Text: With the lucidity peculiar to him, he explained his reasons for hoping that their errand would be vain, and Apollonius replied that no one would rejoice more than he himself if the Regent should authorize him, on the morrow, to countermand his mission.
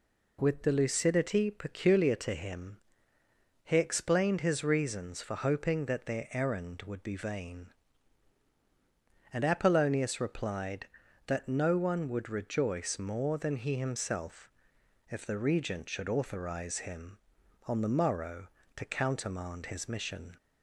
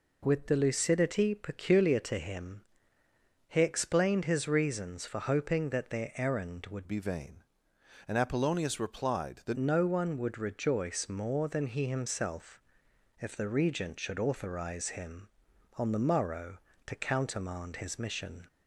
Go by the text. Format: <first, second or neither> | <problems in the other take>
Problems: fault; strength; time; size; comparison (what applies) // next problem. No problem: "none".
first | changes voice from "be" to "that"; from 6.8 to 9.5 s; 2.7 s long // pauses between "himself" and "if"; noticeable; at 12.6 s; 0.58 s long; noticeable in the first